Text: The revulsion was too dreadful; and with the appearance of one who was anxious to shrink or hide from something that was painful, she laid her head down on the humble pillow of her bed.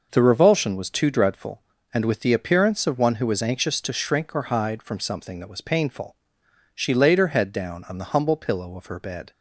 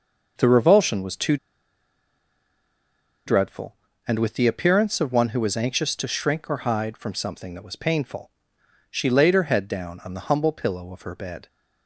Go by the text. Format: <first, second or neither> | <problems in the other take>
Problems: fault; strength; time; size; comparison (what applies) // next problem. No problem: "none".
first | pauses between "too" and "dreadful"; strong; at 1.3 s; 1.9 s long